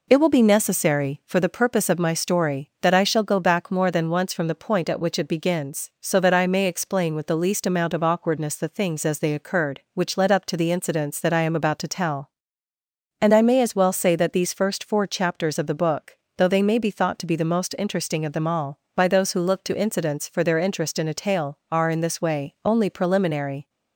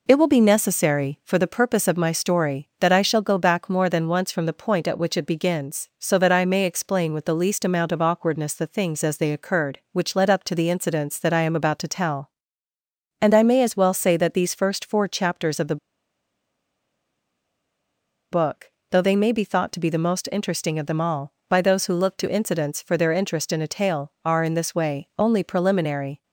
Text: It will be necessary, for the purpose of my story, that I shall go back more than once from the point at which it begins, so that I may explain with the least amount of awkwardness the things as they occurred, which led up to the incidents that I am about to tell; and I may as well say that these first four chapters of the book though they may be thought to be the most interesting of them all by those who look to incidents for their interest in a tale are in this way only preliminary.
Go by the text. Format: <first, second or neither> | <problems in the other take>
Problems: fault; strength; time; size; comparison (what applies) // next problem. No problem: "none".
first | pauses between "the" and "book"; strong; at 15.7 s; 2.5 s long // pauses between "book" and "though"; slight; at 18.7 s; 0.20 s long; slight in the first